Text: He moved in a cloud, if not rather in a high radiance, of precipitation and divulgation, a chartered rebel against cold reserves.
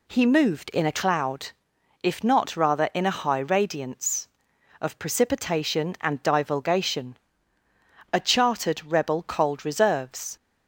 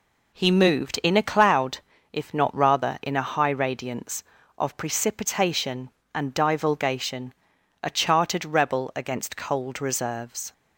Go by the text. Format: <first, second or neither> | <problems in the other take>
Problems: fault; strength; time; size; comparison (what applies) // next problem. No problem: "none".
second | skips "against"; at 9.2 s